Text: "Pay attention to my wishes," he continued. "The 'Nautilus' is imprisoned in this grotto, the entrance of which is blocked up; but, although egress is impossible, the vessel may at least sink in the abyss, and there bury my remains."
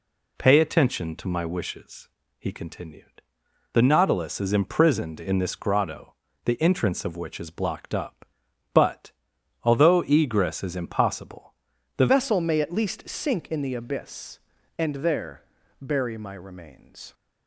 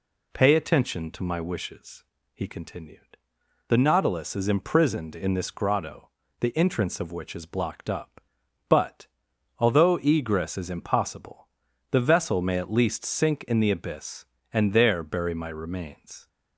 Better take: second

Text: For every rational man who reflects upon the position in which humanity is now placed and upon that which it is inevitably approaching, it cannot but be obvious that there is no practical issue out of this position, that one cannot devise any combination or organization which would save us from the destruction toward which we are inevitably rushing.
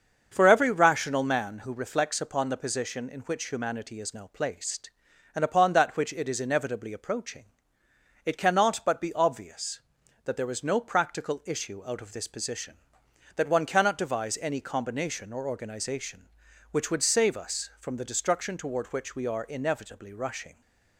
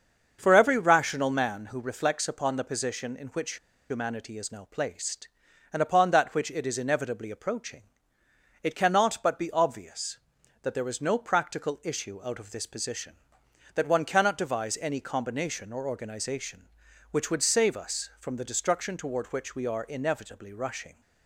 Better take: first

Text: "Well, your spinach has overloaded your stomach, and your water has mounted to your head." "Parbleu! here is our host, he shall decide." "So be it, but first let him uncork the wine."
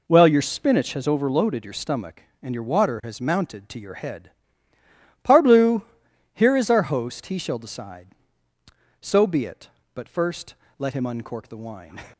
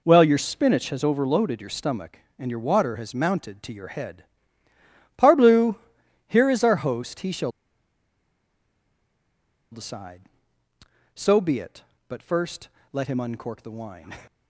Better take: first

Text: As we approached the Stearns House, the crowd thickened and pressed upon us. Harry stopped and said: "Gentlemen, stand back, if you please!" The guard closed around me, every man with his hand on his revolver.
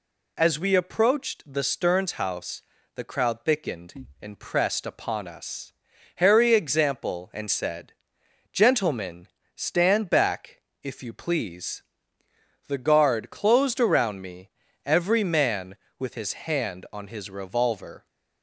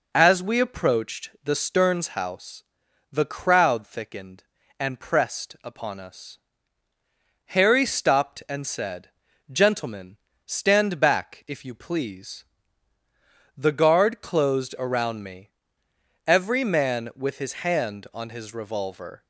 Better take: second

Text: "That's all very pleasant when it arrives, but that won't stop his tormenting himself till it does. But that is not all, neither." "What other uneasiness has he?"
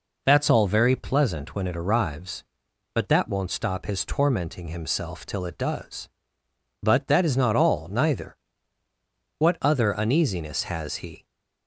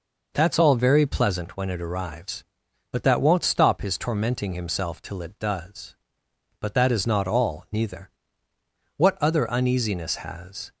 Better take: first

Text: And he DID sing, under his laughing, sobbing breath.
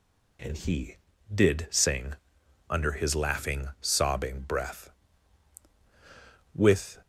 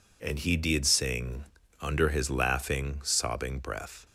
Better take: second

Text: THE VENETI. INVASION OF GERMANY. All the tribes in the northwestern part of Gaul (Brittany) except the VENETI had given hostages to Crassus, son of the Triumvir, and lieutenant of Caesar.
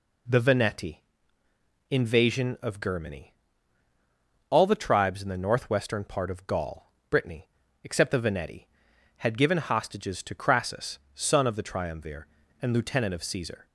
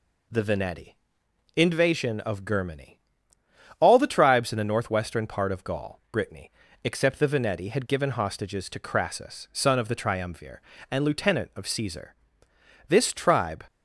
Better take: first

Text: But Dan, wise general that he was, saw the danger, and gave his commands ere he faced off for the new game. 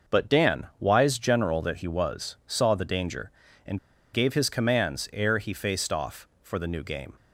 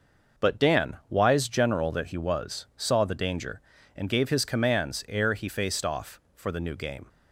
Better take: second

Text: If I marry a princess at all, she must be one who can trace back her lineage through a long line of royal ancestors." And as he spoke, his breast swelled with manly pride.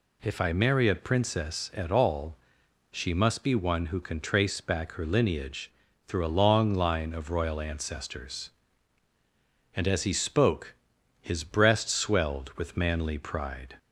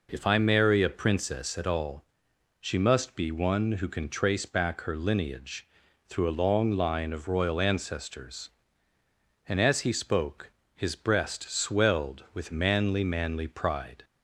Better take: first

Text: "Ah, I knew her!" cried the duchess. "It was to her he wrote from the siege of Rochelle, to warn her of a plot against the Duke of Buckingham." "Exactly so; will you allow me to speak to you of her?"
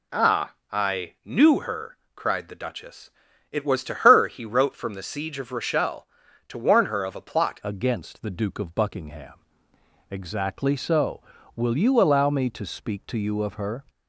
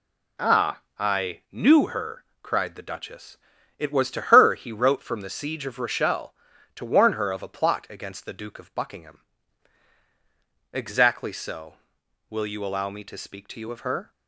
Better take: second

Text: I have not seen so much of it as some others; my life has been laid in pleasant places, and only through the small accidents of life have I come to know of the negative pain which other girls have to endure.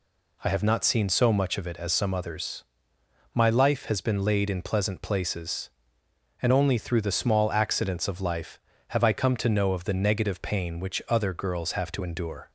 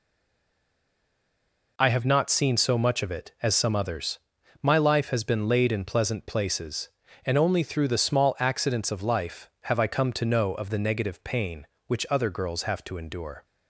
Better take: first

